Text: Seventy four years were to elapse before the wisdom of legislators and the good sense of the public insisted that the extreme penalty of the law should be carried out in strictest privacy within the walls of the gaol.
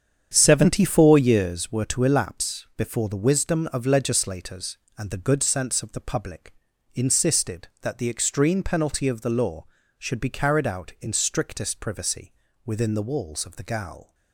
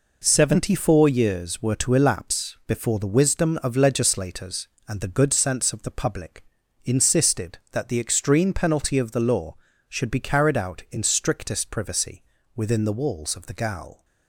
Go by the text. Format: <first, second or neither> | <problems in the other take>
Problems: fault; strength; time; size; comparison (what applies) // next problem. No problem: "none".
second | starts louder than the rest; strong; until 1.7 s; 8 dB // pauses between "public" and "insisted"; at 6.5 s; 0.40 s long; also in the second // pauses between "privacy" and "within"; slight; at 12.3 s; 0.32 s long; slight in the second